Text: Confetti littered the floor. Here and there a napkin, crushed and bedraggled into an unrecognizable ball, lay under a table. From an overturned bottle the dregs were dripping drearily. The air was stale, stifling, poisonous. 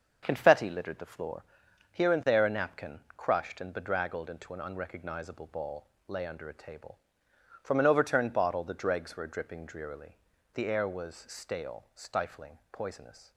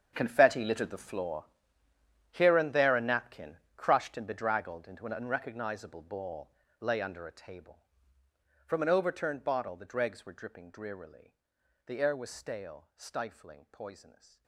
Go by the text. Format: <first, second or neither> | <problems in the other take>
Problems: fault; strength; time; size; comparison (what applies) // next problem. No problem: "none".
first | gets quieter; strong; throughout; 16.5 dB // starts louder than the rest; strong; until 1.1 s; 7.5 dB; also in the first